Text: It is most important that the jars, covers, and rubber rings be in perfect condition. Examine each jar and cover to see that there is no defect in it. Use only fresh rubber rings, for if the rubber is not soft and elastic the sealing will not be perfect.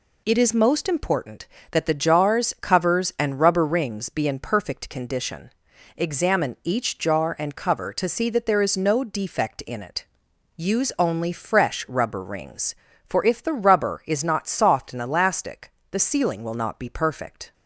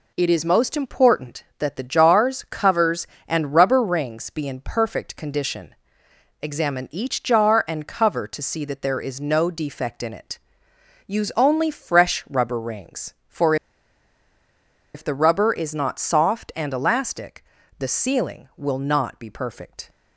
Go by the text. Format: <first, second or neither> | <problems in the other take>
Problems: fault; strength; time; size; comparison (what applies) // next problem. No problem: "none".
first | pauses between "for" and "if"; strong; at 13.5 s; 1.3 s long // pauses between "elastic" and "the"; slight; at 17.4 s; 0.36 s long; slight in the first